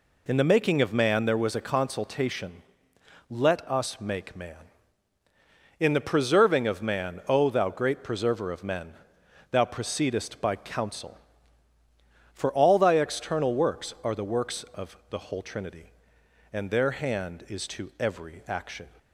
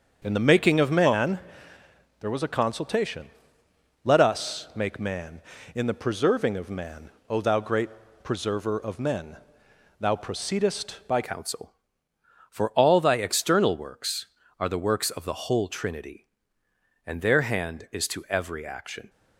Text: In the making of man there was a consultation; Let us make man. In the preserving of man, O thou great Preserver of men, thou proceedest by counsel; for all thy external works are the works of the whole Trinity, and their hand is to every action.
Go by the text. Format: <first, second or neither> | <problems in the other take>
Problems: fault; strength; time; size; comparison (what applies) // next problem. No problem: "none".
first | starts louder than the rest; until 1.2 s; 7 dB // pauses between "man" and "there"; noticeable; at 1.3 s; 0.82 s long // pauses between "great" and "Preserver"; slight; at 7.8 s; 0.34 s long // changes voice at "counsel"; from 11.2 s on; 7.8 s long